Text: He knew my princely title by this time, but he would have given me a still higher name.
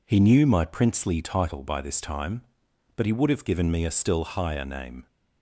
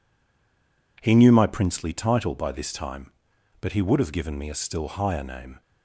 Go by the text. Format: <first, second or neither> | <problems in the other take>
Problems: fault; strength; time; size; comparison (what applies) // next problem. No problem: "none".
first | stays silent before the first word; slight; until 0.9 s; 0.9 s long